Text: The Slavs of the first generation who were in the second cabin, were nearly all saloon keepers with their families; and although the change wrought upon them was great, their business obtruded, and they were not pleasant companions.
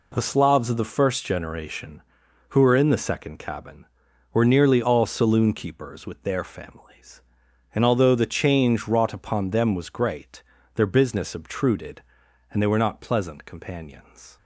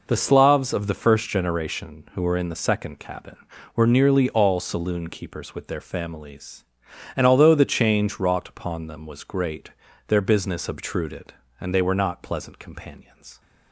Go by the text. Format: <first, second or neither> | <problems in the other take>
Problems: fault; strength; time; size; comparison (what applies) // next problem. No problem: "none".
neither | none